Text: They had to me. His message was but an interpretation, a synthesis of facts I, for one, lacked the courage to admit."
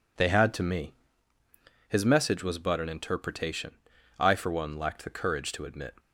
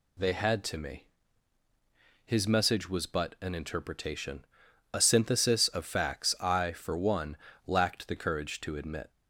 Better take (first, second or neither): second